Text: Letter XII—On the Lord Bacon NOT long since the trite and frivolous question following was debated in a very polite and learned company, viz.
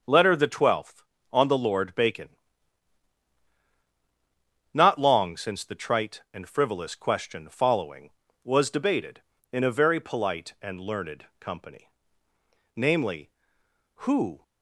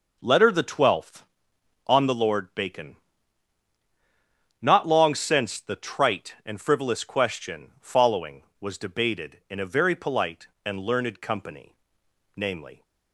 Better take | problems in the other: second | starts louder than the rest; until 1.0 s; 6 dB // pauses between "Bacon" and "NOT"; strong; at 2.3 s; 2.4 s long; strong in the second // goes on to say "Who"; slight; from 13.9 s on; 0.44 s long

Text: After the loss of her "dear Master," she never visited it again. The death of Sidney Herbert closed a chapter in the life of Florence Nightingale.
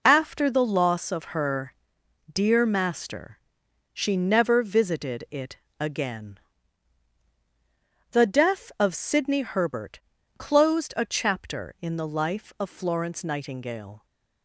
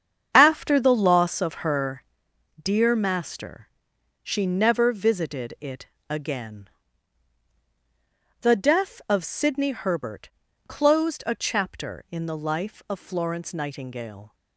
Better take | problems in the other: first | starts louder than the rest; strong; until 1.9 s; 7.5 dB // pauses between "her" and "dear"; noticeable; at 2.0 s; 0.58 s long; noticeable in the first // pauses between "it" and "again"; slight; at 5.8 s; 0.24 s long; slight in the first // pauses between "Herbert" and "closed"; at 10.2 s; 0.40 s long; also in the first

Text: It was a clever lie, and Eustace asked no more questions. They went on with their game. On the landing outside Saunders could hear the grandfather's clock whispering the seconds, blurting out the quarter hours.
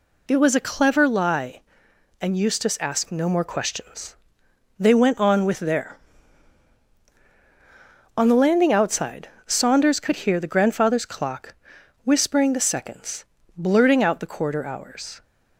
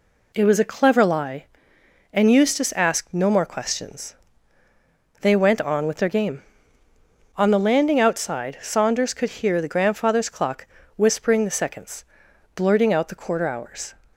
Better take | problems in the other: second | skips "game"; at 7.0 s // pauses between "outside" and "Saunders"; slight; at 9.2 s; 0.18 s long // pauses between "clock" and "whispering"; noticeable; at 11.5 s; 0.50 s long; slight in the second

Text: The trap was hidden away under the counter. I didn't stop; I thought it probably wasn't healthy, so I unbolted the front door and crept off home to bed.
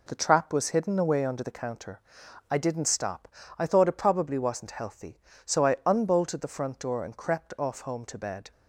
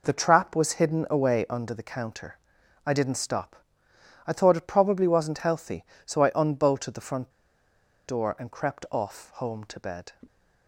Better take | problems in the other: first | pauses between "front" and "door"; noticeable; at 7.3 s; 0.76 s long

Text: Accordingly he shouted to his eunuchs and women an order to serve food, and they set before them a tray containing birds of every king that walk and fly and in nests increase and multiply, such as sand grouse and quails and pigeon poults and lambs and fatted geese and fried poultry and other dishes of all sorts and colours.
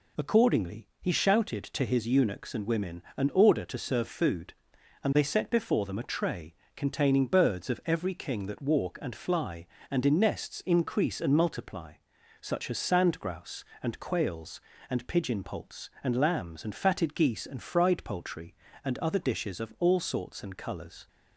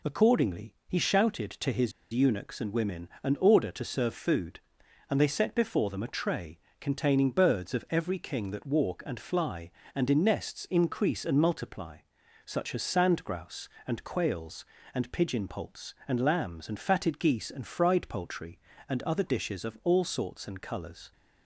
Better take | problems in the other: first | pauses between "his" and "eunuchs"; slight; at 1.9 s; 0.21 s long // pauses between "tray" and "containing"; slight; at 6.5 s; 0.22 s long; slight in the first

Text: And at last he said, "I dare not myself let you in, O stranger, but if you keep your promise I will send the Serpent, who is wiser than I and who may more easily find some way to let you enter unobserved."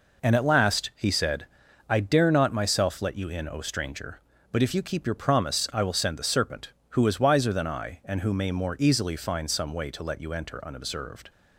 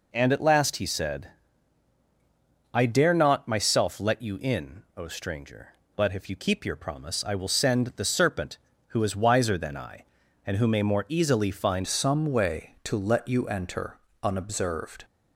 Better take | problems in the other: first | changes voice at "some"; from 11.8 s on; 3.2 s long // pauses between "enter" and "unobserved"; slight; at 13.9 s; 0.28 s long

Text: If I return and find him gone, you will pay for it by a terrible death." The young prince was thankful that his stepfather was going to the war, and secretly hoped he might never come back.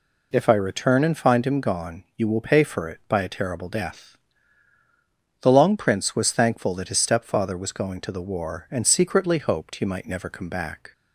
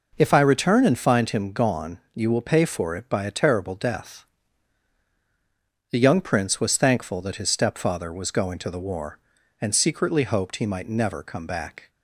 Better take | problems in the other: second | says "long" for "young"; at 5.5 s

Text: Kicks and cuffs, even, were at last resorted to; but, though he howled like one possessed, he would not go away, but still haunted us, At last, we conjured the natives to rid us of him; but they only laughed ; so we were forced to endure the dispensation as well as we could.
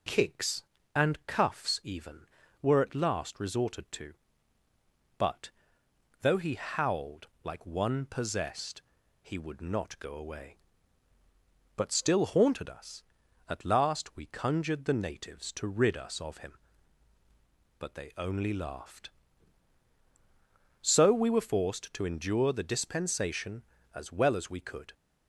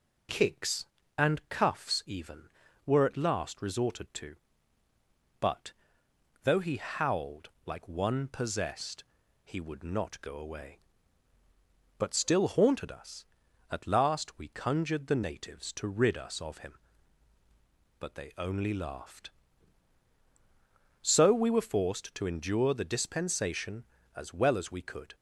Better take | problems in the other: neither | pauses between "howled" and "like"; slight; the same in both

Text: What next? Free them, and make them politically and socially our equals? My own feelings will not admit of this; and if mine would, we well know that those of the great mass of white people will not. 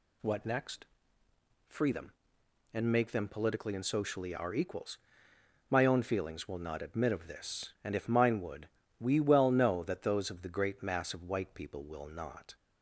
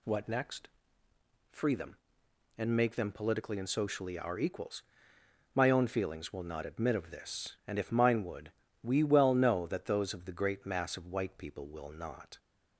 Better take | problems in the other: neither | none

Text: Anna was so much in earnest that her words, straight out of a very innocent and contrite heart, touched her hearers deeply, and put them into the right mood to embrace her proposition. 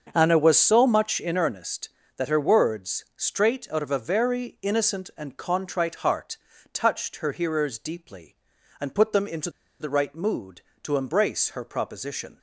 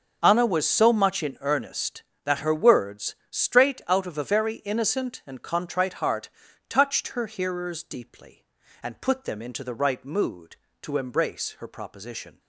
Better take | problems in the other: second | starts louder than the rest; until 1.1 s; 7 dB; also in the second // pauses between "into" and "the"; slight; at 9.4 s; 0.30 s long

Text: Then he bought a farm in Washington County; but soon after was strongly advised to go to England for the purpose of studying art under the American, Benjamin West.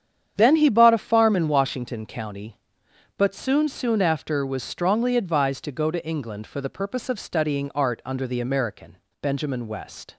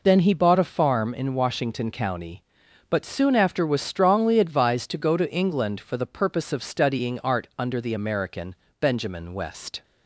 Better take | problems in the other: second | starts louder than the rest; strong; until 1.3 s; 8.5 dB // says "soon" twice; at 3.6 s

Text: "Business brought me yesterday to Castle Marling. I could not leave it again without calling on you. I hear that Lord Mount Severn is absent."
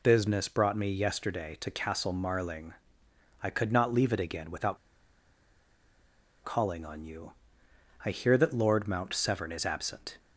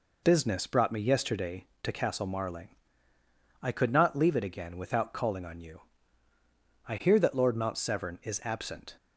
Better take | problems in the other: second | pauses between "without" and "calling"; strong; at 4.7 s; 1.6 s long

